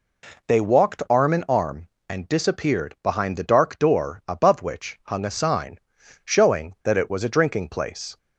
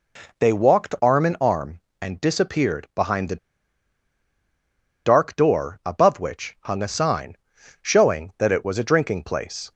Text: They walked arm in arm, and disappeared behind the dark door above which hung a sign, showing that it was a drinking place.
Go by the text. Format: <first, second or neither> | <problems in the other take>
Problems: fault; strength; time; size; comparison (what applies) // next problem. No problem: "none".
first | pauses between "the" and "dark"; strong; at 3.3 s; 1.6 s long